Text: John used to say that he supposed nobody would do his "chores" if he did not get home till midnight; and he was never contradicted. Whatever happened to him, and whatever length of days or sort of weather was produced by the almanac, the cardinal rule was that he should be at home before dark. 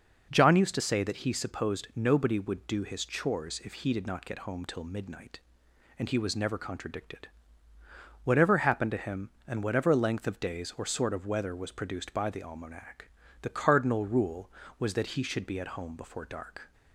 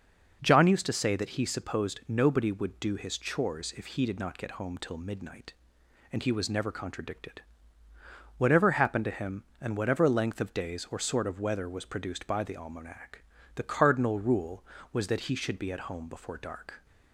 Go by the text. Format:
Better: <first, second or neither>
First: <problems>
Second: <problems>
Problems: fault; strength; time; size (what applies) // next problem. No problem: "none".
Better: neither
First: none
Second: none